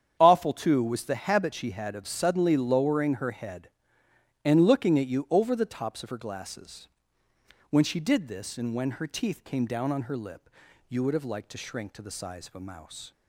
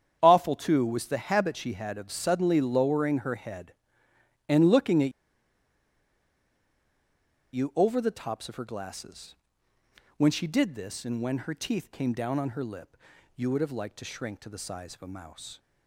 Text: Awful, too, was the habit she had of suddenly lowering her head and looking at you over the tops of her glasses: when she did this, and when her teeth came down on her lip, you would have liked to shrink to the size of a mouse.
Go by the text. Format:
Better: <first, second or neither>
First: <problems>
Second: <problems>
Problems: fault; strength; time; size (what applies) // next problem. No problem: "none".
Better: first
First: starts louder than the rest; strong; until 1.1 s; 8.5 dB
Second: starts louder than the rest; strong; until 1.2 s; 8.5 dB // pauses between "at" and "you"; strong; at 5.1 s; 2.4 s long